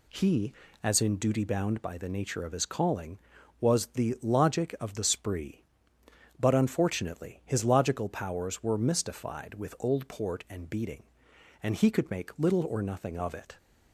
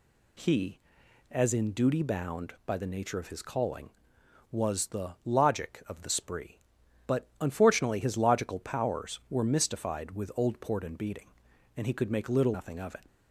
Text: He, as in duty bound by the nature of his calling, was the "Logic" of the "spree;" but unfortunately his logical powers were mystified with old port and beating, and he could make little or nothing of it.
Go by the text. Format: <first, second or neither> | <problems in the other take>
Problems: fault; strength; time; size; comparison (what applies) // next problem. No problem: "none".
first | skips "or"; at 12.5 s